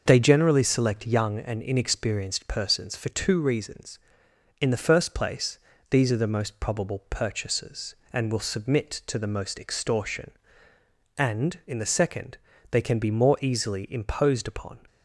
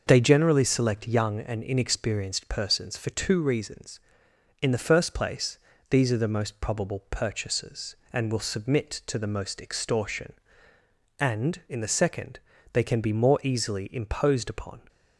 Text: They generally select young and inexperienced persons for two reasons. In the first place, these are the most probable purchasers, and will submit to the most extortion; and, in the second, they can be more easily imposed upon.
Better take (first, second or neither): neither